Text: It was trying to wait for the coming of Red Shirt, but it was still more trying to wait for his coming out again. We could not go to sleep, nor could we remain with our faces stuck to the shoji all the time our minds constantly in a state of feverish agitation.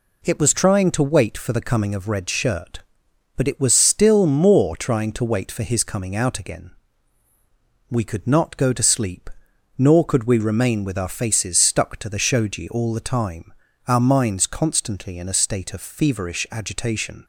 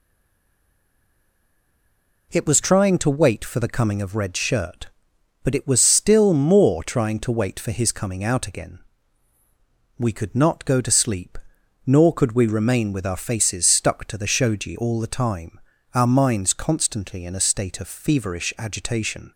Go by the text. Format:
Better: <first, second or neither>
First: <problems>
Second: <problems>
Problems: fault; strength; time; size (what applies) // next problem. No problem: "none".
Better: first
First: pauses between "time" and "our"; slight; at 13.5 s; 0.34 s long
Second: stays silent before the first word; until 2.3 s; 2.3 s long // pauses between "time" and "our"; slight; at 15.5 s; 0.34 s long